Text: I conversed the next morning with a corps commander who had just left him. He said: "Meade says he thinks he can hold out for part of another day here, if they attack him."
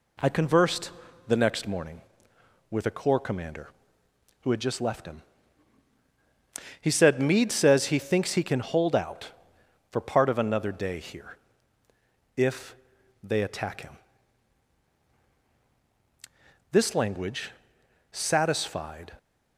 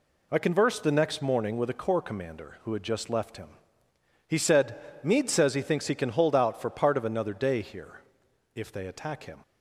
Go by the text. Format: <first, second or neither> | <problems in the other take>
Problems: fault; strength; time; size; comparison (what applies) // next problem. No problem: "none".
second | pauses between "conversed" and "the"; slight; at 0.9 s; 0.36 s long // pauses between "if" and "they"; noticeable; at 12.7 s; 0.48 s long // goes on to say "This language satisfied"; strong; from 16.7 s on; 2.4 s long